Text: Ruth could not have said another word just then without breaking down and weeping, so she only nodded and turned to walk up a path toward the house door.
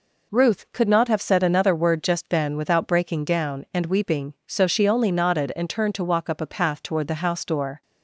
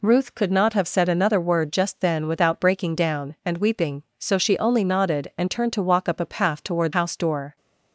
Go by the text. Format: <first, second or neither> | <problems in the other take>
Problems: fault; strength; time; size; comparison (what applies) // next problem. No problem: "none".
first | skips "the"; at 6.9 s